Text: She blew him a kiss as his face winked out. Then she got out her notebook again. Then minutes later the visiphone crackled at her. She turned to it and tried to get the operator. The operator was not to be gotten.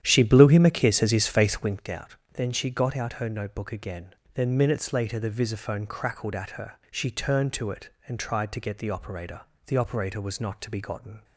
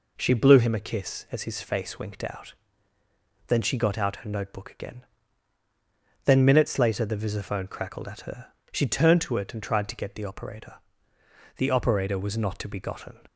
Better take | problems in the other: second | starts louder than the rest; strong; until 1.9 s; 10.5 dB

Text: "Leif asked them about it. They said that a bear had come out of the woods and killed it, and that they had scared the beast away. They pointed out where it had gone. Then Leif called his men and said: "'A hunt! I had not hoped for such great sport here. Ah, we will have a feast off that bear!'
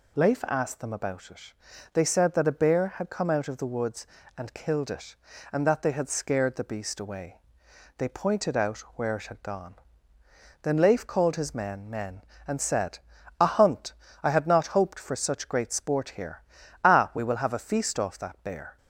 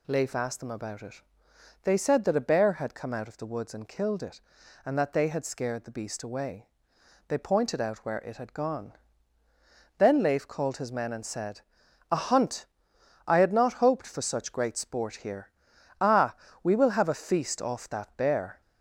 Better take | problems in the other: second | pauses between "out" and "where"; slight; at 8.7 s; 0.18 s long // says "men" twice; at 11.8 s

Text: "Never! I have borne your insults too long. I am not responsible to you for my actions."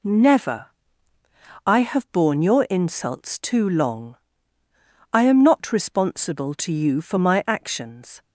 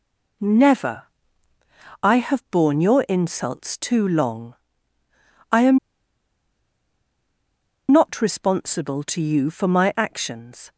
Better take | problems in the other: first | pauses between "am" and "not"; strong; at 5.7 s; 2.1 s long

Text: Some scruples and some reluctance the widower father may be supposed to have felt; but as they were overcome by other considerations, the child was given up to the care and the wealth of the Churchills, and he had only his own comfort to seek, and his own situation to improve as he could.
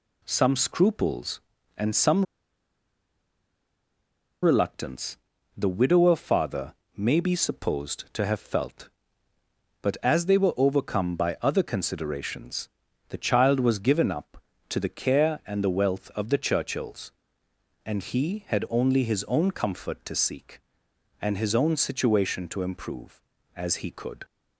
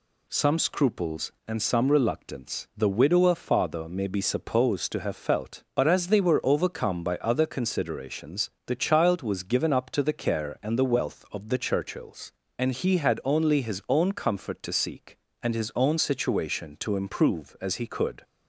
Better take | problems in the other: second | pauses between "some" and "reluctance"; strong; at 2.2 s; 2.1 s long // pauses between "reluctance" and "the"; at 5.1 s; 0.40 s long // pauses between "father" and "may"; slight; at 6.7 s; 0.22 s long

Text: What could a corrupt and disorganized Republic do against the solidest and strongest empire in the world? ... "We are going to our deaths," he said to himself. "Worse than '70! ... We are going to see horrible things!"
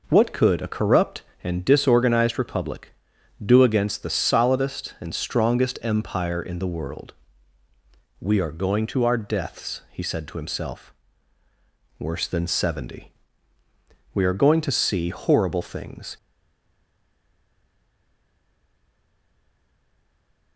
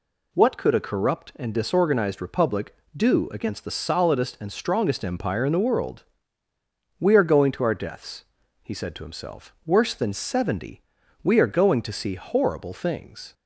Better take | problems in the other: second | stays silent after the last word; strong; from 16.1 s on; 4.4 s long

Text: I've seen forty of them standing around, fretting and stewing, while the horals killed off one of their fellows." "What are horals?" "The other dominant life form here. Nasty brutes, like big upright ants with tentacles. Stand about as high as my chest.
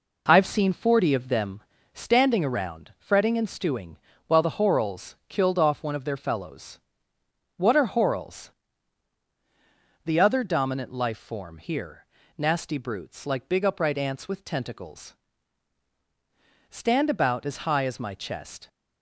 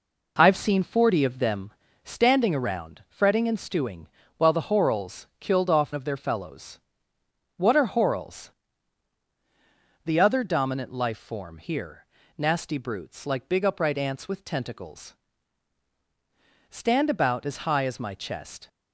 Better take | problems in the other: first | pauses between "them" and "standing"; slight; at 1.7 s; 0.32 s long; slight in the first // skips "one"; at 5.9 s

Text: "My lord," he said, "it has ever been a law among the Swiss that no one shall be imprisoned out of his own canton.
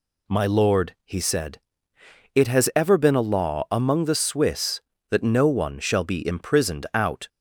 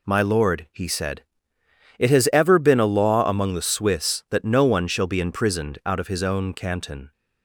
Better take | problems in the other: second | stops before "of his own canton"; at 7.2 s

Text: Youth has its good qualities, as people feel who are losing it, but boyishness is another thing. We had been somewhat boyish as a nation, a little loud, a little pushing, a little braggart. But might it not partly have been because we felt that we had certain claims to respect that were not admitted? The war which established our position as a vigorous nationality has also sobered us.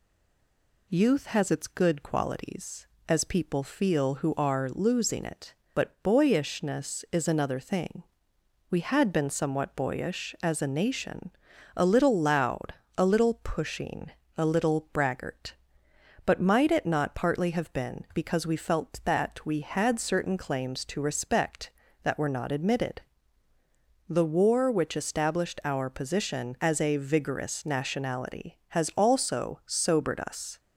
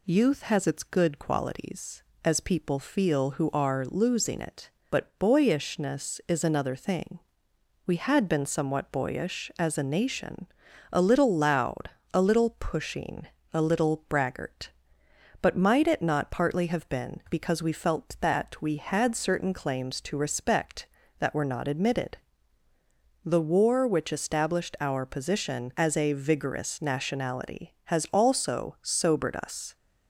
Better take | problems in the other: second | stays silent before the first word; slight; until 0.8 s; 0.8 s long

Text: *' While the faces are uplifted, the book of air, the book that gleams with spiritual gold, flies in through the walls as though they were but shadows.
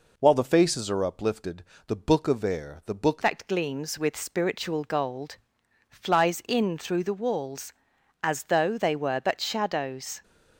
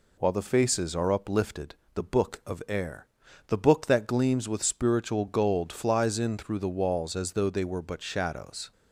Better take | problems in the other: second | changes voice at "that"; from 3.2 s on; 7.0 s long

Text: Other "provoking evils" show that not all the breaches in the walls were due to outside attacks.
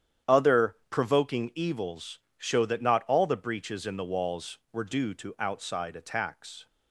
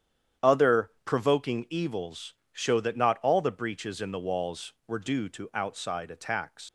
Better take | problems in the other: first | starts louder than the rest; strong; until 1.5 s; 9.5 dB; strong in the first // pauses between "evils" and "show"; slight; at 2.3 s; 0.20 s long; slight in the first // leaves "attacks" unfinished; at 6.6 s; 115 ms

